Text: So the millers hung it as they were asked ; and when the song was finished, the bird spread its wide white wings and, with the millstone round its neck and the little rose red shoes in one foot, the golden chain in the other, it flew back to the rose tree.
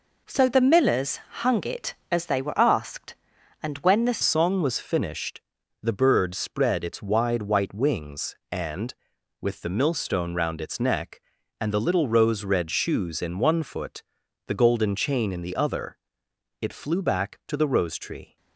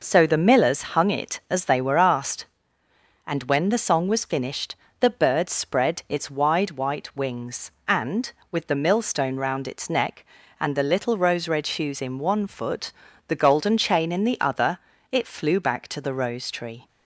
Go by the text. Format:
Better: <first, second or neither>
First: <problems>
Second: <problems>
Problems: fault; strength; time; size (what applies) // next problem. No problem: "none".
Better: second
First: pauses between "millers" and "hung"; slight; at 1.1 s; 0.26 s long // changes voice at "song"; from 4.2 s on; 14.1 s long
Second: none